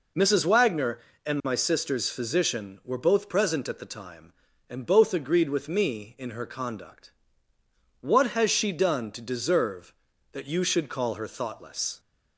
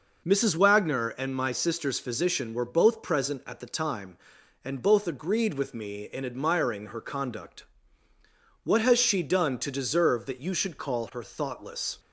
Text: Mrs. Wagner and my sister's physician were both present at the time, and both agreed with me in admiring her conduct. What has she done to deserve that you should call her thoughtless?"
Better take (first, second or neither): second